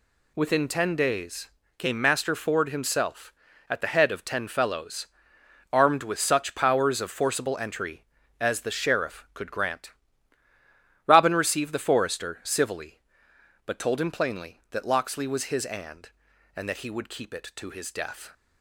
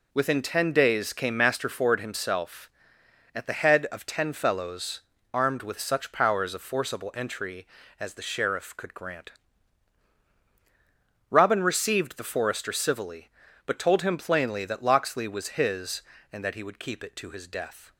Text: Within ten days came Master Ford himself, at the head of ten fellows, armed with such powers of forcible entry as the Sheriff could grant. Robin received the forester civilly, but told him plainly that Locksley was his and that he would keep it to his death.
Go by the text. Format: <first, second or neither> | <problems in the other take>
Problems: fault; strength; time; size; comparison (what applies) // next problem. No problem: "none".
second | pauses between "days" and "came"; slight; at 1.4 s; 0.28 s long // says "and" twice; at 16.5 s